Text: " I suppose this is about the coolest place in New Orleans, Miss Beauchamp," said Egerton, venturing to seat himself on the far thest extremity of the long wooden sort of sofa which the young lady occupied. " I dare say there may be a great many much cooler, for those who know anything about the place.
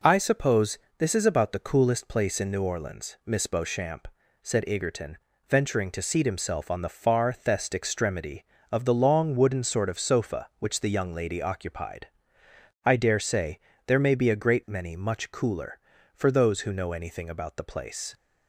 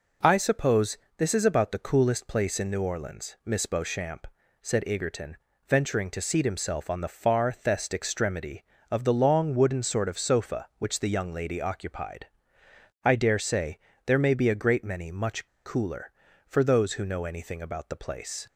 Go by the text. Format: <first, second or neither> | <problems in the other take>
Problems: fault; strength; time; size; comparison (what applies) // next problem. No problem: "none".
first | pauses between "suppose" and "this"; slight; at 0.9 s; 0.20 s long; slight in the first // pauses between "say" and "there"; slight; at 13.7 s; 0.26 s long; slight in the first // pauses between "much" and "cooler"; slight; at 15.4 s; 0.17 s long